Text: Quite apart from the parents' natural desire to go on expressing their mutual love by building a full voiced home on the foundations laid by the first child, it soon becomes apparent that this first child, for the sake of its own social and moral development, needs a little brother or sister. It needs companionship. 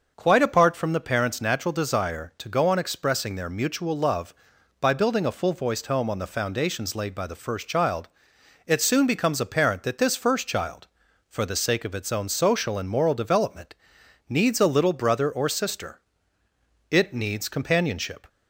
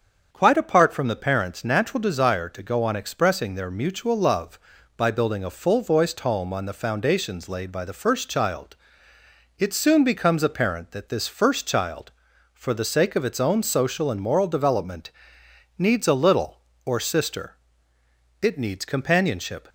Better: first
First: starts louder than the rest; until 1.1 s; 6.5 dB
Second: starts louder than the rest; strong; until 1.3 s; 7 dB // skips "brother"; at 16.7 s

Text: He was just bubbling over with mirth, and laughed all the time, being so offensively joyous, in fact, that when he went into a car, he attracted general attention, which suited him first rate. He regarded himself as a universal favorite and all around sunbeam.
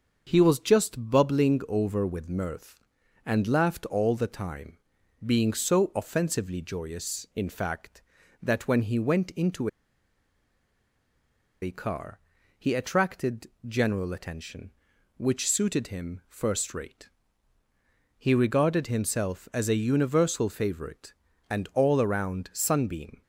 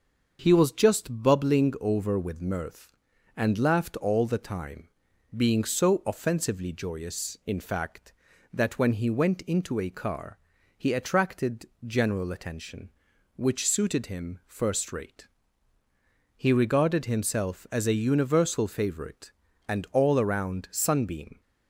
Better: second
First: starts louder than the rest; until 1.2 s; 6.5 dB // pauses between "into" and "a"; strong; at 9.6 s; 1.9 s long // pauses between "attracted" and "general"; slight; at 13.4 s; 0.18 s long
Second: starts louder than the rest; until 1.4 s; 6.5 dB // pauses between "attracted" and "general"; slight; at 11.6 s; 0.18 s long

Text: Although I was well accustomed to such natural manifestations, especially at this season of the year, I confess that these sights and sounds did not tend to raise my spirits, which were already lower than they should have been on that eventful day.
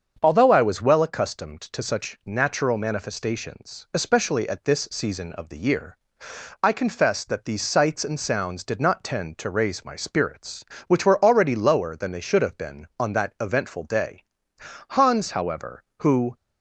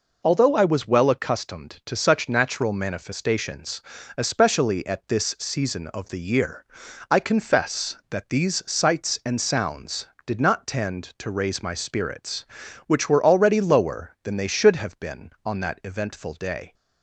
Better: second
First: starts louder than the rest; until 1.2 s; 7 dB // goes on to say "Hans however who"; from 14.8 s on; 1.4 s long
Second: none

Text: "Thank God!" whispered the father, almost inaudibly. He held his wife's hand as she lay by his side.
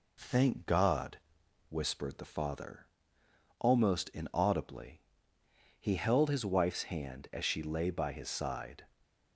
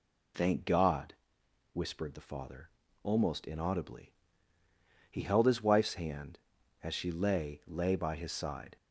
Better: first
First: none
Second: says "lay" twice; at 7.6 s

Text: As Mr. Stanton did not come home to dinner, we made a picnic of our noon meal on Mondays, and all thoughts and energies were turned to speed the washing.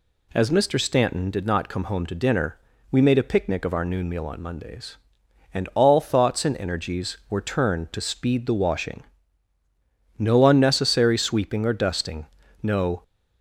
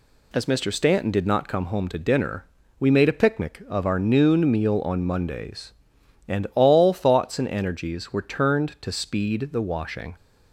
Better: second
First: goes on to say "No unnecessary sweeping or dusting no"; strong; from 10.1 s on; 2.8 s long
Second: none

